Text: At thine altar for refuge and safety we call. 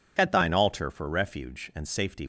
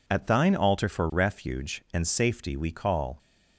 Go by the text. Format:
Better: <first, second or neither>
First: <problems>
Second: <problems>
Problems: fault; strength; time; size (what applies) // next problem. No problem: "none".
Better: second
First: stops before "we call"; at 2.2 s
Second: none